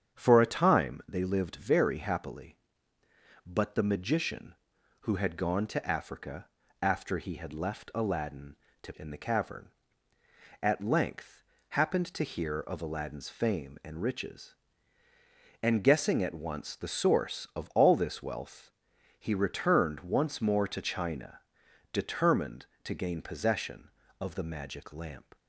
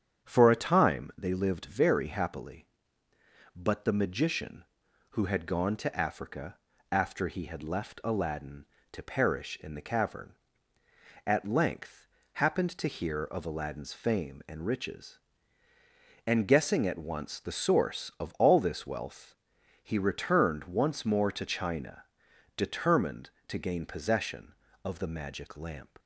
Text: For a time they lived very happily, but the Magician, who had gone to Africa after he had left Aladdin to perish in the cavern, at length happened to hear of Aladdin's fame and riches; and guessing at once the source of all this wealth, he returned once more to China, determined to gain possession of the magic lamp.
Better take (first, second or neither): second